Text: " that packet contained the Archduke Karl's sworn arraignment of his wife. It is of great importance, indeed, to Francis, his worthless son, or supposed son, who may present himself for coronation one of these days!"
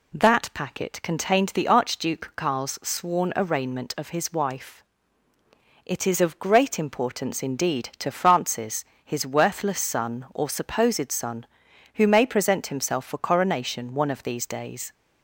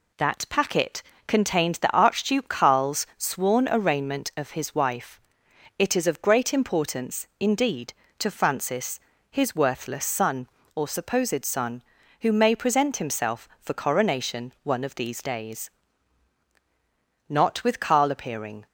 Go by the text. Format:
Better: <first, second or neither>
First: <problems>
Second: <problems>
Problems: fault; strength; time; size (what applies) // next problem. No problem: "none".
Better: first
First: none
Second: pauses between "packet" and "contained"; slight; at 1.0 s; 0.24 s long // goes on to say "Not with Karl appearing"; from 17.2 s on; 1.3 s long